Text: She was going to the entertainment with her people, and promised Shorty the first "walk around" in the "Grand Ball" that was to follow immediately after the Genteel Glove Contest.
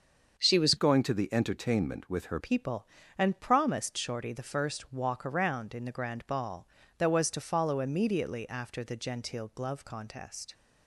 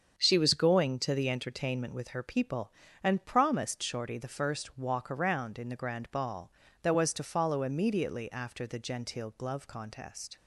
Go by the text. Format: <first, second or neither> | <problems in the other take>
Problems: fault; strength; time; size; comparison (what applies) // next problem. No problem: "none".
second | starts louder than the rest; until 1.4 s; 6.5 dB; strong in the second // changes voice from "going" to "her"; from 0.7 to 2.3 s; 1.6 s long